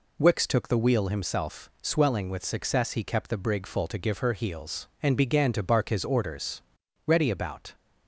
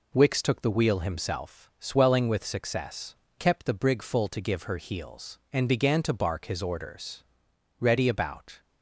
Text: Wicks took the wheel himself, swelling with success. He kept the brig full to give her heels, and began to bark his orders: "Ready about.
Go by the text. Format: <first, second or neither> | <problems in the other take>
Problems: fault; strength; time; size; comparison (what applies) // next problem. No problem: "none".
first | skips "He"; at 3.2 s